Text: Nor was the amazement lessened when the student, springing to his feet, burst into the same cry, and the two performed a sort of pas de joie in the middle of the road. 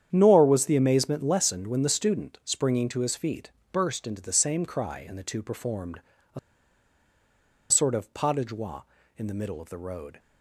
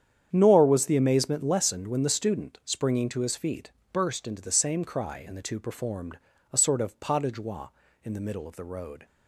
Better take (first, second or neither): second